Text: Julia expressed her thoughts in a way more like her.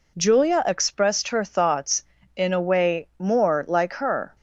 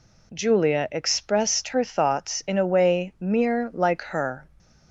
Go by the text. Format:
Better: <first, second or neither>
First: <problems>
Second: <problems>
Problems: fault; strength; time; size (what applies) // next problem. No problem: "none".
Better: first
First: none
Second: says "mere" for "more"; at 3.2 s